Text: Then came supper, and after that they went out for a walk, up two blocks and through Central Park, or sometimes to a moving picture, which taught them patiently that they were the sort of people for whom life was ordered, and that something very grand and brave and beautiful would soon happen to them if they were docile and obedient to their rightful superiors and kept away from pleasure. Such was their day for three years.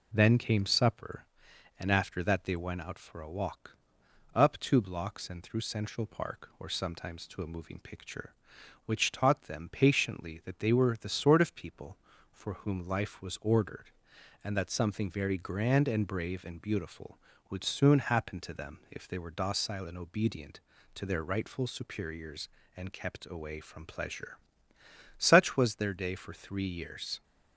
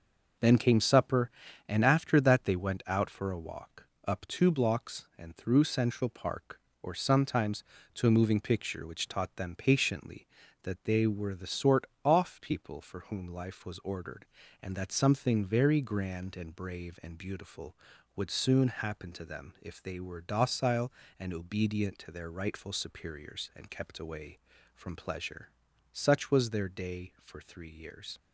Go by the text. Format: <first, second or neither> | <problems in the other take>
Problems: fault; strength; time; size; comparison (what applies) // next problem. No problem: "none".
first | says "off" for "of"; at 12.0 s